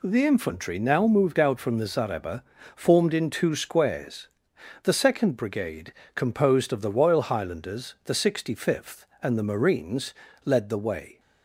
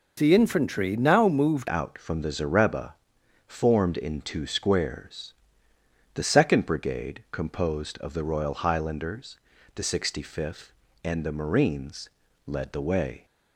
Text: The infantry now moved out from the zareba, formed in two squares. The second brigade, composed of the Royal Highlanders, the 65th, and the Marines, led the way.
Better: first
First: none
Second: changes voice at "out"; from 1.6 s on; 11.6 s long

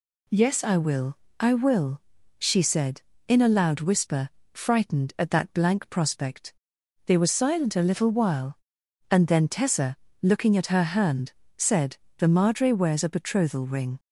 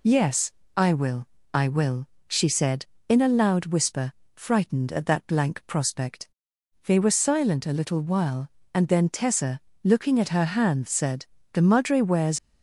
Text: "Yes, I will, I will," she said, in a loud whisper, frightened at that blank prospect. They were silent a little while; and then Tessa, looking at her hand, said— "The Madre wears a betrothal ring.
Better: first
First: none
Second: stops before "a betrothal ring"; at 12.3 s

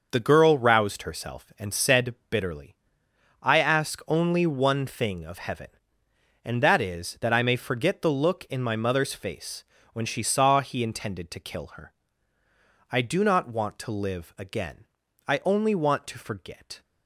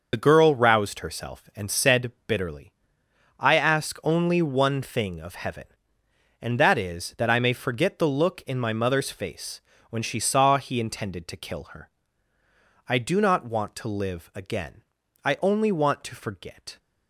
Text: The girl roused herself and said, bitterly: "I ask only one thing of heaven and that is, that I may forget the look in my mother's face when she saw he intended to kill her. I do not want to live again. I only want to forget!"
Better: first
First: starts louder than the rest; noticeable; until 1.1 s; 6 dB // pauses between "face" and "when"; slight; at 9.6 s; 0.30 s long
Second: loses the start of "The"; at 0.1 s; 35 ms // starts louder than the rest; noticeable; until 1.1 s; 6 dB // pauses between "face" and "when"; slight; at 9.6 s; 0.30 s long

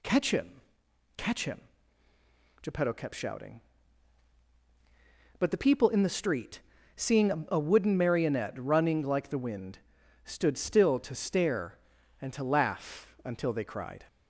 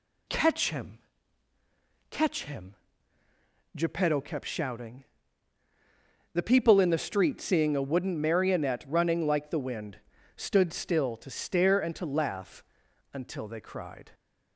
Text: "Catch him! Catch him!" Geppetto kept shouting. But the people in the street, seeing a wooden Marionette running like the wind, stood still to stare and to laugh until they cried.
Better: first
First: none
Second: skips "But"; at 5.6 s // pauses between "laugh" and "until"; noticeable; at 12.6 s; 0.52 s long

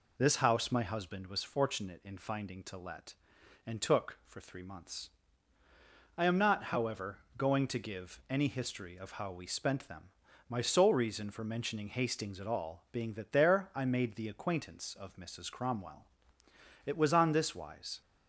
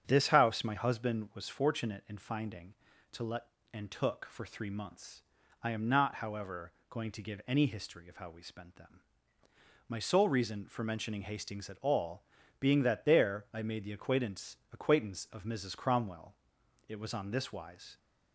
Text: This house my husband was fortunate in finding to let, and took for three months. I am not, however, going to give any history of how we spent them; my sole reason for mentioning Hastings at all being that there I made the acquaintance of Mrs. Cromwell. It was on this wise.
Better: first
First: none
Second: starts louder than the rest; strong; until 1.0 s; 7.5 dB // pauses between "all" and "being"; at 12.2 s; 0.38 s long // says "acquaintance" twice; at 14.7 s

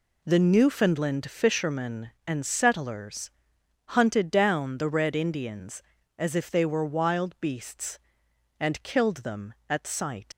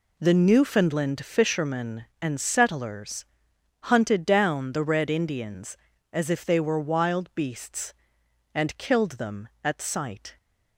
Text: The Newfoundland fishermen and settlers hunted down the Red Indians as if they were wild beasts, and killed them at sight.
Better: second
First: pauses between "settlers" and "hunted"; noticeable; at 3.3 s; 0.56 s long // leaves "sight" unfinished; at 10.3 s; 100 ms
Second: pauses between "settlers" and "hunted"; noticeable; at 3.2 s; 0.56 s long

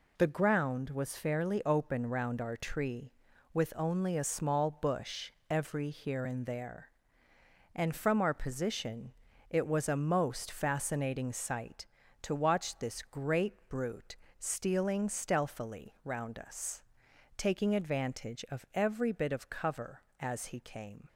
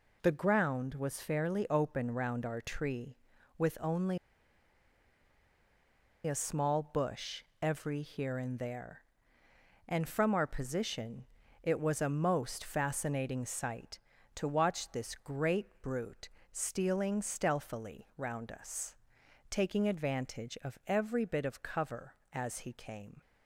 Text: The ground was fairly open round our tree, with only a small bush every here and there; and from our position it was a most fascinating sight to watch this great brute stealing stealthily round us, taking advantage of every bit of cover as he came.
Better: first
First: pauses between "bush" and "every"; slight; at 5.3 s; 0.18 s long // pauses between "position" and "it"; at 9.1 s; 0.38 s long // pauses between "great" and "brute"; slight; at 13.5 s; 0.16 s long // pauses between "brute" and "stealing"; slight; at 14.1 s; 0.22 s long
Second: pauses between "only" and "a"; strong; at 4.1 s; 2.0 s long // pauses between "bush" and "every"; slight; at 7.4 s; 0.18 s long // pauses between "position" and "it"; at 11.2 s; 0.38 s long // pauses between "great" and "brute"; slight; at 15.6 s; 0.16 s long // pauses between "brute" and "stealing"; slight; at 16.2 s; 0.22 s long

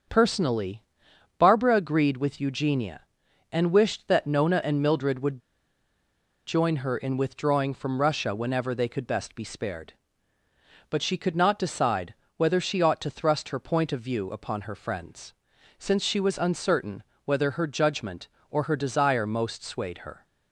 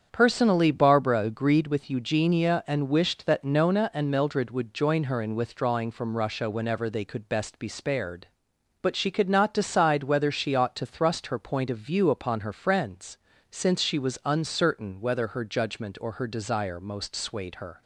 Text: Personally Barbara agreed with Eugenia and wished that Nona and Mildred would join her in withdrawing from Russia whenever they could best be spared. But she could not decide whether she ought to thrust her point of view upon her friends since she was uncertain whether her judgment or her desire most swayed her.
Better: second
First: starts louder than the rest; until 1.6 s; 7 dB // pauses between "Personally" and "Barbara"; noticeable; at 0.8 s; 0.56 s long // pauses between "would" and "join"; at 5.3 s; 1.0 s long // pauses between "decide" and "whether"; slight; at 12.1 s; 0.24 s long // pauses between "friends" and "since"; noticeable; at 15.3 s; 0.46 s long // pauses between "uncertain" and "whether"; slight; at 17.0 s; 0.20 s long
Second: starts louder than the rest; strong; until 1.1 s; 8 dB // pauses between "friends" and "since"; slight; at 13.1 s; 0.34 s long

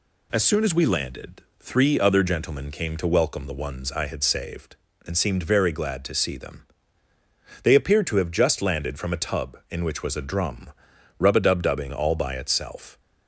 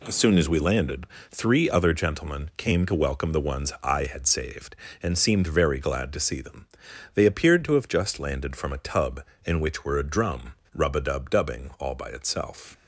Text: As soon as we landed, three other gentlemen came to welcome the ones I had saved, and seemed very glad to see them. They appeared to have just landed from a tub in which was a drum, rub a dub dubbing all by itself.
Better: first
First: none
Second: says "were" for "was"; at 9.8 s

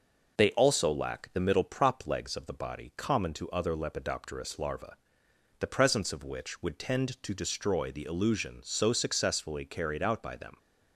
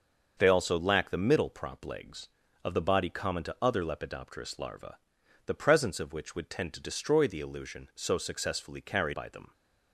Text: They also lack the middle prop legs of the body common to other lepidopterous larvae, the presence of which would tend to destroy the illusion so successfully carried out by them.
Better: first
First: none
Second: starts louder than the rest; until 1.3 s; 6.5 dB // skips "out"; at 9.1 s

